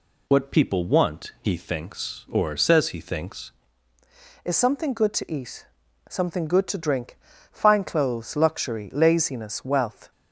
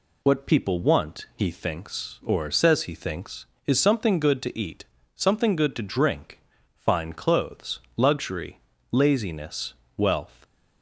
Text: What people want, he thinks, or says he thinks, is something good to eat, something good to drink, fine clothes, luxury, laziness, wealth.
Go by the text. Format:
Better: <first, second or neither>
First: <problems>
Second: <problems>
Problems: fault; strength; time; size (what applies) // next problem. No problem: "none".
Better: second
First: changes voice at "is"; from 4.4 s on; 5.7 s long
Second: none